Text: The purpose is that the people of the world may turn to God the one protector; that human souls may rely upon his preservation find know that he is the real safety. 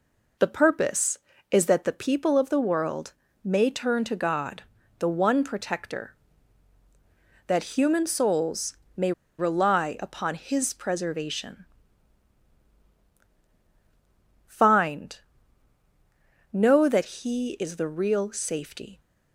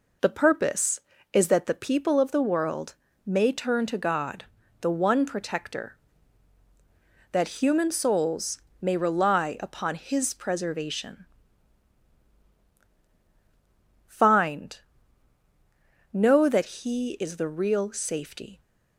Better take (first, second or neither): second